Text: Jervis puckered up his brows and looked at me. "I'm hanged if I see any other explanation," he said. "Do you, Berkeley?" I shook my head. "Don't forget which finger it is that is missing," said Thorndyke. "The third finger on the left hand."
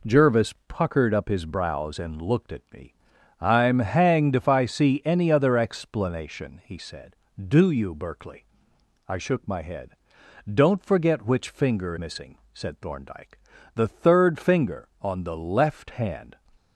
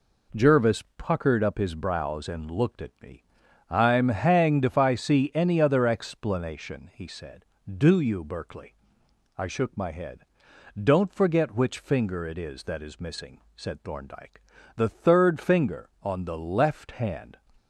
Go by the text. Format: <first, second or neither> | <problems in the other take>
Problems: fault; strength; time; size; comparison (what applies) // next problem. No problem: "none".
second | skips "it is that is"; at 11.9 s